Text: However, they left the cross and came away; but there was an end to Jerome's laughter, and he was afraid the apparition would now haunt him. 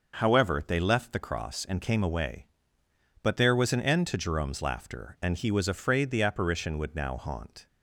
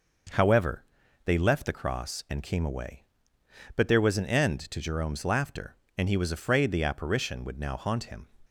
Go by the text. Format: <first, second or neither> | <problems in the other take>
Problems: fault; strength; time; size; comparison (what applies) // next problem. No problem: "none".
second | starts louder than the rest; noticeable; until 1.2 s; 6 dB // stops before "him"; at 7.6 s